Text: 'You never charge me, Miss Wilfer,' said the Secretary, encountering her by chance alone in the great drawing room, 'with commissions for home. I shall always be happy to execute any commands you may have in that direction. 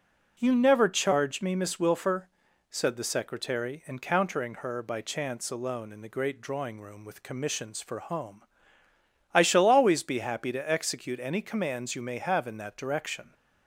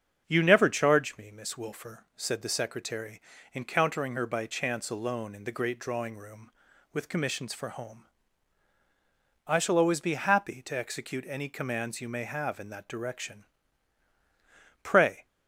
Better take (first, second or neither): first